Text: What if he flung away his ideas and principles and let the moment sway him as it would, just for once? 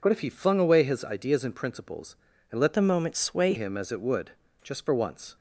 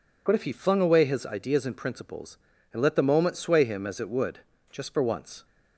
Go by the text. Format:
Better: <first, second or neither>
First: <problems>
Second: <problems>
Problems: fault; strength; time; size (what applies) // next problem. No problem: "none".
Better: second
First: changes voice from "the" to "sway"; from 2.7 to 3.5 s; 0.8 s long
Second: none